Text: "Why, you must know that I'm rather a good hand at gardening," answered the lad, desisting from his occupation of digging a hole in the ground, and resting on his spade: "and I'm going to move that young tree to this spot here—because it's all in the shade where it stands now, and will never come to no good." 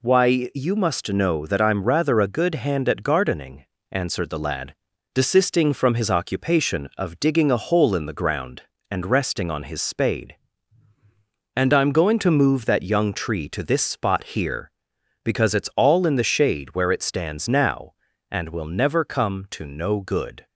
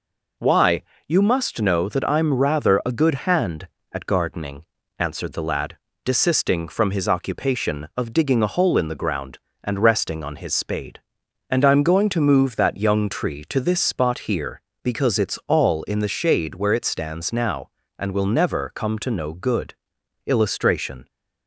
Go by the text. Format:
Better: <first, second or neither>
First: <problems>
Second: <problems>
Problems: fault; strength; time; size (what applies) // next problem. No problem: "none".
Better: first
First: none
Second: goes on to say "Illustration"; noticeable; from 20.2 s on; 0.82 s long